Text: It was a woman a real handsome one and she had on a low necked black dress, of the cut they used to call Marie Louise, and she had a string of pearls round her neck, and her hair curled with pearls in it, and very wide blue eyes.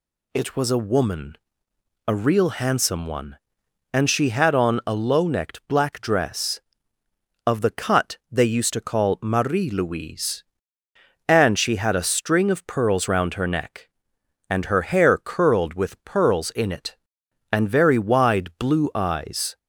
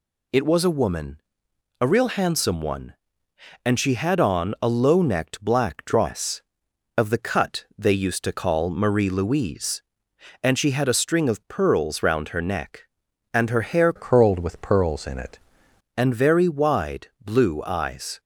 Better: first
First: pauses between "woman" and "a"; noticeable; at 1.3 s; 0.70 s long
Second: pauses between "woman" and "a"; noticeable; at 1.2 s; 0.60 s long // changes voice from "curled" to "it"; from 13.9 to 15.3 s; 1.4 s long // pauses between "wide" and "blue"; slight; at 17.0 s; 0.16 s long

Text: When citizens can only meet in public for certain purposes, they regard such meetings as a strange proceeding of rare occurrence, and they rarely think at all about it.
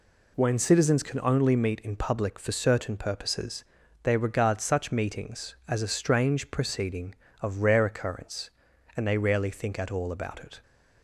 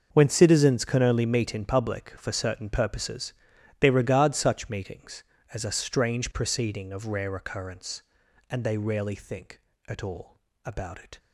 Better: first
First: none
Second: gets quieter; strong; throughout; 14 dB // pauses between "all" and "about"; slight; at 10.3 s; 0.26 s long

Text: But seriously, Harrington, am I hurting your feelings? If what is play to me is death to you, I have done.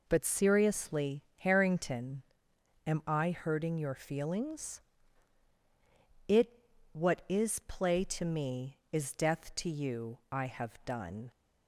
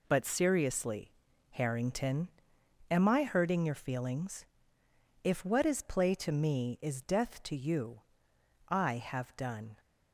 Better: second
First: says "It" for "If"; at 6.2 s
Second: none

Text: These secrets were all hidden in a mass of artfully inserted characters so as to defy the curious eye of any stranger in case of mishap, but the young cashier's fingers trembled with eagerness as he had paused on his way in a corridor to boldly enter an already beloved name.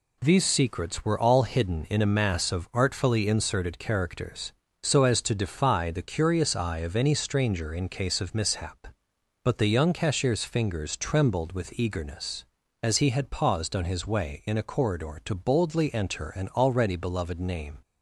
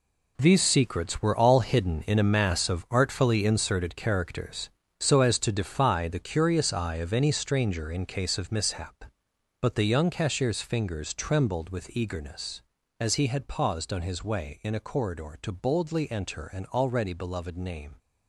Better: first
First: none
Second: gets quieter; strong; throughout; 11 dB

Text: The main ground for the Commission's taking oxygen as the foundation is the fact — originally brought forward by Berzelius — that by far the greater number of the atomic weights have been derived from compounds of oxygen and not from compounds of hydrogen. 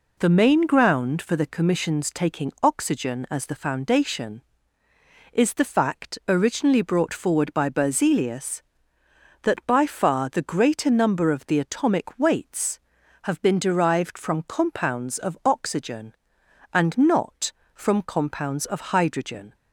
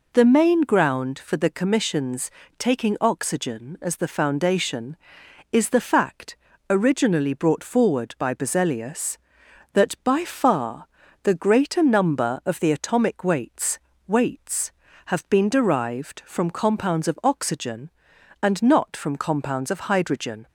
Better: first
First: none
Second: pauses between "Commission's" and "taking"; slight; at 2.2 s; 0.28 s long // pauses between "far" and "the"; at 10.8 s; 0.38 s long // says "weights" twice; at 14.0 s

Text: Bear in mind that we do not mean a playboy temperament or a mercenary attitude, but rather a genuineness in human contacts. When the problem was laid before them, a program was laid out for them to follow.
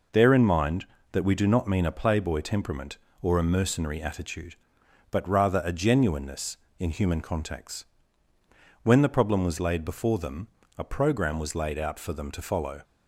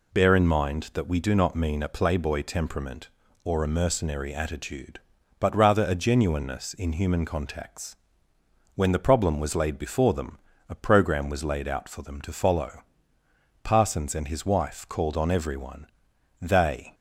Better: first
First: none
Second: goes on to say "Parsons and his wife called on everyone they"; strong; from 13.6 s on; 3.3 s long

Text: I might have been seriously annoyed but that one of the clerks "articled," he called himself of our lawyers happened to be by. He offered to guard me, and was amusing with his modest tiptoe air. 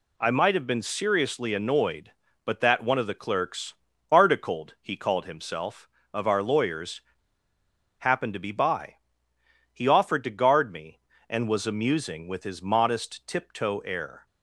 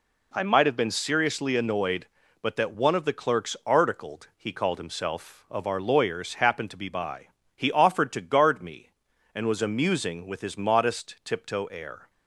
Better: second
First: pauses between "clerks" and "articled"; slight; at 3.7 s; 0.36 s long // pauses between "lawyers" and "happened"; noticeable; at 7.0 s; 0.96 s long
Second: none

